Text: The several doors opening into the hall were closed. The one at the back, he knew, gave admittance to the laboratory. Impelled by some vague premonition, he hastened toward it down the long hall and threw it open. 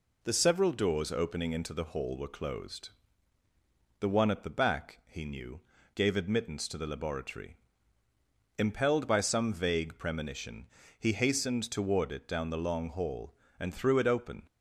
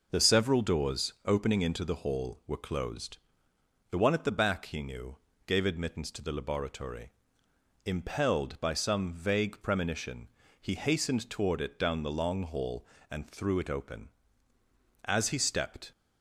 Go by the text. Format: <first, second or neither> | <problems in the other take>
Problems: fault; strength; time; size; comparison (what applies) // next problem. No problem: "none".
first | goes on to say "As he stepped"; noticeable; from 15.0 s on; 0.88 s long